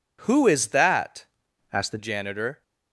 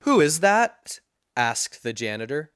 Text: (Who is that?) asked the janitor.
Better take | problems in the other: second | changes voice from "asked" to "the"; from 1.7 to 1.9 s; 0.2 s long

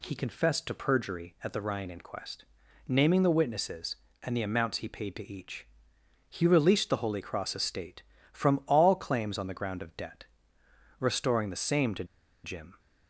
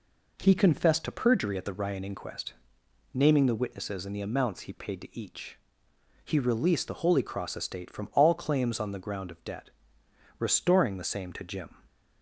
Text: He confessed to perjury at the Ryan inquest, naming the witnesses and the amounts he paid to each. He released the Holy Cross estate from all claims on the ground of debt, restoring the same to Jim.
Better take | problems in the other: second | pauses between "to" and "Jim"; at 12.0 s; 0.40 s long

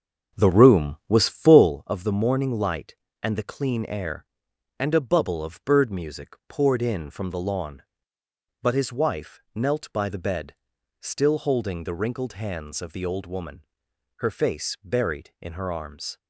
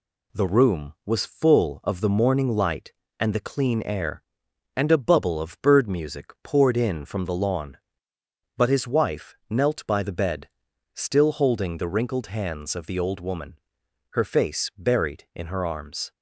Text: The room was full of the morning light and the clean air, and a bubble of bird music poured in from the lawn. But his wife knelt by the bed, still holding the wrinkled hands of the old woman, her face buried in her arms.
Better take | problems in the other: second | starts louder than the rest; until 1.8 s; 6.5 dB

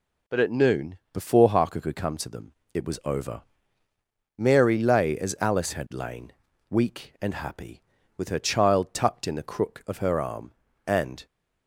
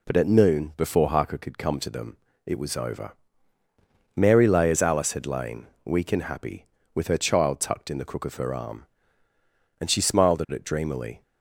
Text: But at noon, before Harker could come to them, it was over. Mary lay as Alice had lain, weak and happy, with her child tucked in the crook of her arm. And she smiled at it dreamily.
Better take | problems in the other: second | stops before "she smiled at it dreamily"; at 11.2 s

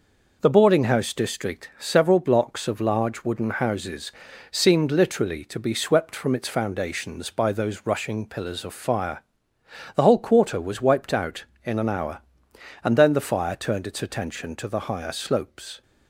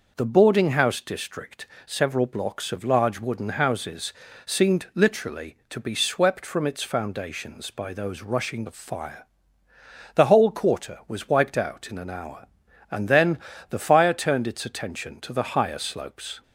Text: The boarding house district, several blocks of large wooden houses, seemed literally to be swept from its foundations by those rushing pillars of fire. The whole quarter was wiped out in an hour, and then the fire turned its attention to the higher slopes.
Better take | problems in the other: first | skips "pillars"; at 8.6 s // pauses between "then" and "the"; slight; at 13.3 s; 0.32 s long

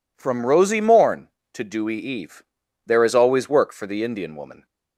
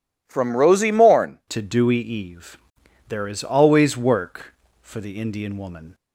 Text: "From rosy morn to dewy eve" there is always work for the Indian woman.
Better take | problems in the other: first | changes voice at "to"; from 1.4 s on; 4.5 s long // pauses between "eve" and "there"; noticeable; at 2.5 s; 0.50 s long; also in the first

